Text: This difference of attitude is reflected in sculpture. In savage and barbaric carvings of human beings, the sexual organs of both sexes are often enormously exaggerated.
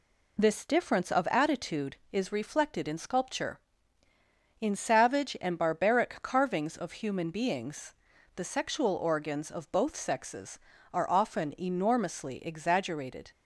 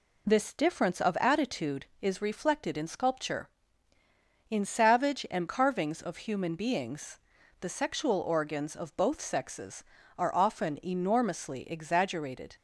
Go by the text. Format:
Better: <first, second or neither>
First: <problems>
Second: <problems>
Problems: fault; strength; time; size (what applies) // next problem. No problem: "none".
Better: first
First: none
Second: skips "barbaric"; at 5.4 s